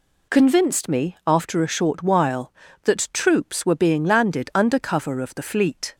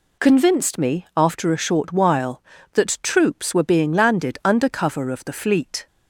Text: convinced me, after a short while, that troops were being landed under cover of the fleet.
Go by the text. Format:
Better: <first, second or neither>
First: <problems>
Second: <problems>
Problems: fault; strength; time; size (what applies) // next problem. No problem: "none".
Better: neither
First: none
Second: none